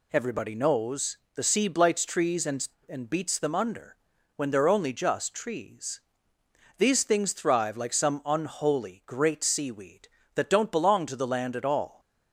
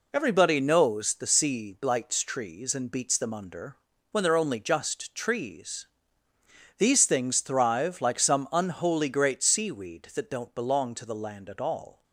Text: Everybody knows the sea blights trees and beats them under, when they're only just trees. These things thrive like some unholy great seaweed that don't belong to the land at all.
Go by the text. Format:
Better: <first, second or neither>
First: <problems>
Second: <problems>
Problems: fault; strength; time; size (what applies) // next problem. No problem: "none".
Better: second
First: pauses between "knows" and "the"; slight; at 1.1 s; 0.18 s long // says "and" twice; at 2.8 s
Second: none